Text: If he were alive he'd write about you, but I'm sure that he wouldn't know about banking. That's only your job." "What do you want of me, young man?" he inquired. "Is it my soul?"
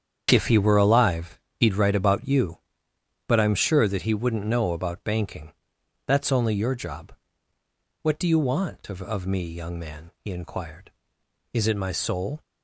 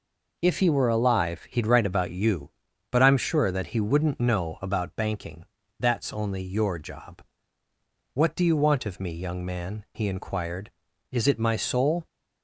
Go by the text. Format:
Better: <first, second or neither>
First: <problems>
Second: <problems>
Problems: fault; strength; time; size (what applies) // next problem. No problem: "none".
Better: second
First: starts louder than the rest; strong; until 1.3 s; 8 dB // pauses between "alive" and "he'd"; slight; at 1.3 s; 0.16 s long // says "of" twice; at 9.0 s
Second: none